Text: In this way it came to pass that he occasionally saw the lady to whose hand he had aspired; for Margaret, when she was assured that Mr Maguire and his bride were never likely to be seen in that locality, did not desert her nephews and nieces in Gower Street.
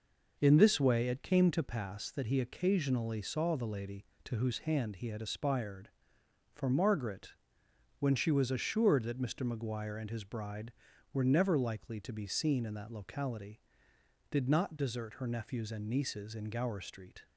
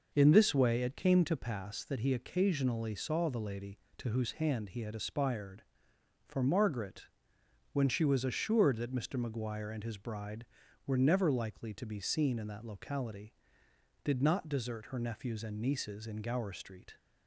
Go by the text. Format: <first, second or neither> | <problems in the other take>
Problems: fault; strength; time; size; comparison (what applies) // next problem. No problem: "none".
neither | none